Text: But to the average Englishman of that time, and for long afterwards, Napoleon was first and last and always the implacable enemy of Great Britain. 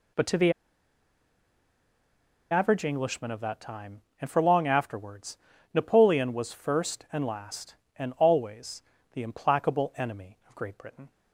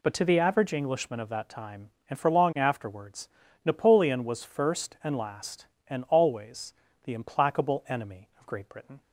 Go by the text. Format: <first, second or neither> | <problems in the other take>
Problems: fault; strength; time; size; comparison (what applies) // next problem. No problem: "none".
second | pauses between "the" and "average"; strong; at 0.5 s; 1.9 s long // pauses between "always" and "the"; slight; at 8.8 s; 0.30 s long; slight in the second